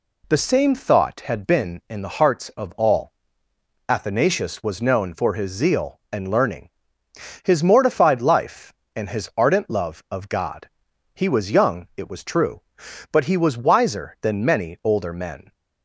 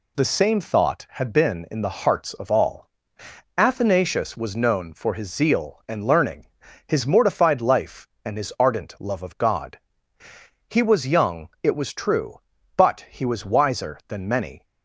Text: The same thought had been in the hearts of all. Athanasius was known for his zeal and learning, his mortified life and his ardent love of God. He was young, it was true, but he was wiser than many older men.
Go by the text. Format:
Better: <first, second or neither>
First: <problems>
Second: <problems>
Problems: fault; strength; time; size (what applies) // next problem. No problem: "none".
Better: first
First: none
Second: stops before "older men"; at 14.6 s